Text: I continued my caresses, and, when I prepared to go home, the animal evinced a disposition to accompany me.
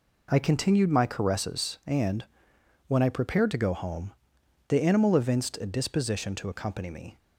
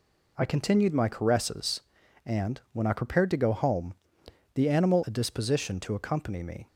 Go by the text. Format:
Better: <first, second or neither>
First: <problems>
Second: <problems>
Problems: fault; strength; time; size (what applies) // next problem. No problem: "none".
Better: first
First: none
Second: skips "evinced"; at 5.0 s